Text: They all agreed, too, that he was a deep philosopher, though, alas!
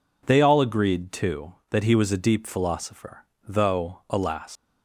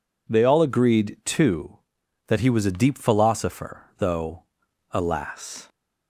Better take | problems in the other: second | leaves "alas" unfinished; at 4.5 s; 145 ms

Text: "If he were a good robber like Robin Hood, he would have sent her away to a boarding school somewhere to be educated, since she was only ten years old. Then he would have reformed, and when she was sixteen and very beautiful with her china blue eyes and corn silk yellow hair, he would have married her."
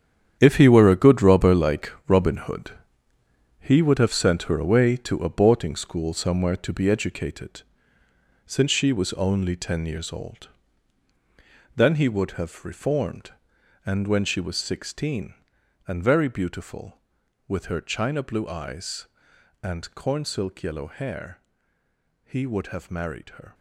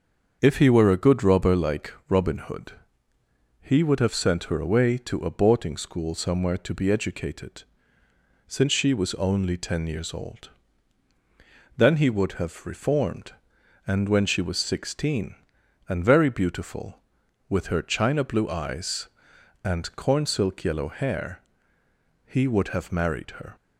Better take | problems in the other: second | gets quieter; strong; throughout; 12 dB // starts louder than the rest; strong; until 1.4 s; 9 dB; also in the second // pauses between "like" and "Robin"; slight; at 1.9 s; 0.16 s long; slight in the second

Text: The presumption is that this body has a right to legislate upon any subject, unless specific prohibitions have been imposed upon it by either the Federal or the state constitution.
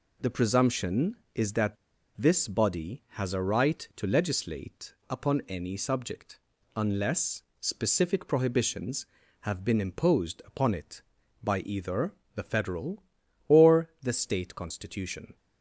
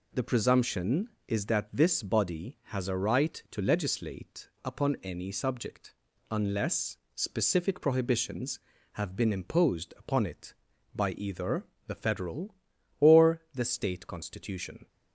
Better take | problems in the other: second | pauses between "that" and "this"; at 1.7 s; 0.42 s long // pauses between "legislate" and "upon"; slight; at 4.9 s; 0.16 s long; slight in the second // pauses between "unless" and "specific"; slight; at 7.4 s; 0.18 s long; slight in the second // pauses between "either" and "the"; slight; at 12.1 s; 0.22 s long; slight in the second

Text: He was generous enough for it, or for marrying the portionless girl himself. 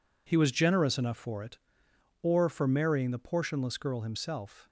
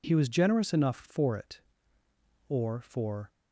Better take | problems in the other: first | stops before "marrying the portionless girl himself"; at 3.3 s

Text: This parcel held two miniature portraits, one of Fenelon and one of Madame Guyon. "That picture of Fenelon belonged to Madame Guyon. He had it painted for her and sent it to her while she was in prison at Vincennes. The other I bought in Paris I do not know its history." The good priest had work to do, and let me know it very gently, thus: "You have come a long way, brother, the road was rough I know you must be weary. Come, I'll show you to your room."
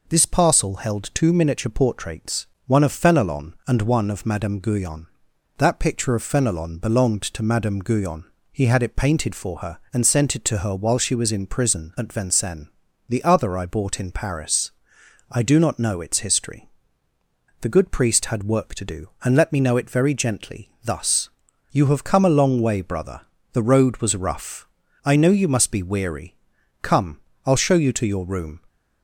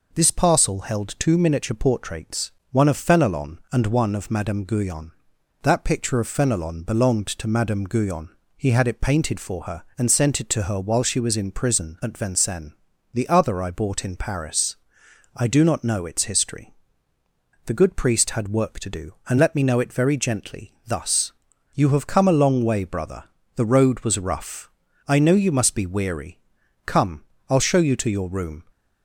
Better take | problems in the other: neither | pauses between "Paris" and "I"; noticeable; the same in both // pauses between "rough" and "I"; the same in both

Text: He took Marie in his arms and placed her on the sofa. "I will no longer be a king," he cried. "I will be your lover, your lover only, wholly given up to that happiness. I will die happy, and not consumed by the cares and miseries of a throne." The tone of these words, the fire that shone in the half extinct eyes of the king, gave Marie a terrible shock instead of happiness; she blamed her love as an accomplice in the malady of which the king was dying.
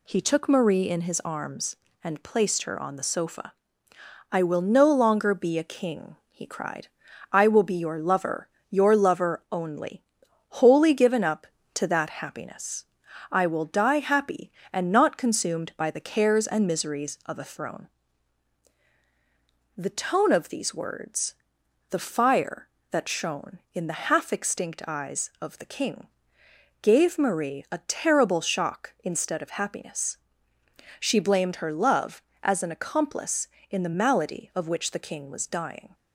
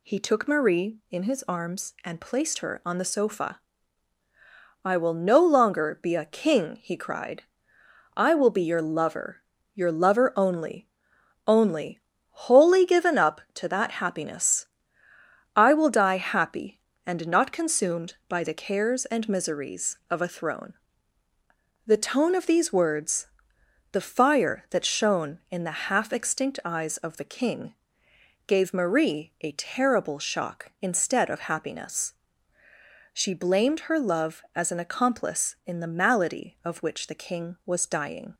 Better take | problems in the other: first | says "only" twice; at 11.4 s

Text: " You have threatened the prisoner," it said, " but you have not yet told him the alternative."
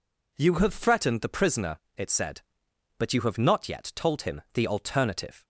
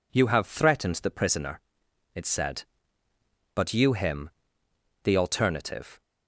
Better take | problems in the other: first | skips "have not yet told"; at 3.9 s // pauses between "him" and "the"; noticeable; at 4.2 s; 0.76 s long

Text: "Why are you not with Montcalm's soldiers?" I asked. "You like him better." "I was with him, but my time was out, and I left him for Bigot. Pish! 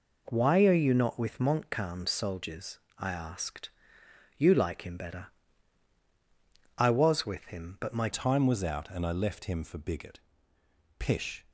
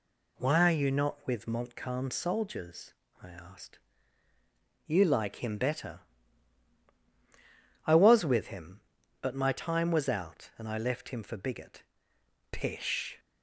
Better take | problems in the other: second | changes voice at "time"; from 8.1 s on; 3.3 s long

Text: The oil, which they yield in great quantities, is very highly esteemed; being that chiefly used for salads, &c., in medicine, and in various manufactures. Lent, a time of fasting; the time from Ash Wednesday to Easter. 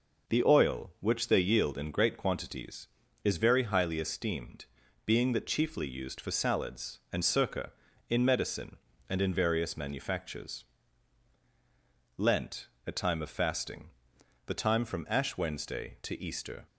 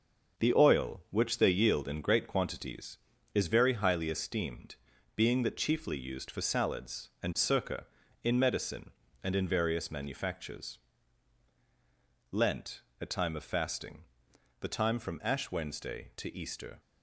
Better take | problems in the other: first | gets quieter; throughout; 7 dB

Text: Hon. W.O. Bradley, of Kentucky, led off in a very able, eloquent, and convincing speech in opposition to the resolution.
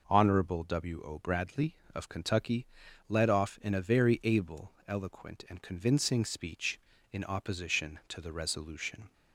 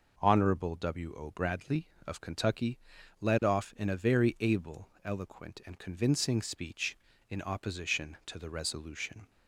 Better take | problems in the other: neither | none

